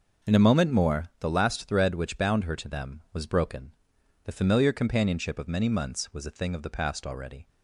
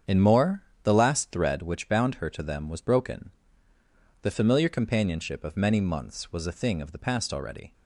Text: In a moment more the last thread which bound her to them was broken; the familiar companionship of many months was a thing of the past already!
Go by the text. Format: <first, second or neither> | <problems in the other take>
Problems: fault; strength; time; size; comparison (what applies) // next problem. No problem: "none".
first | starts louder than the rest; strong; until 1.2 s; 8 dB // skips "a moment"; at 0.2 s // pauses between "more" and "the"; slight; at 0.6 s; 0.20 s long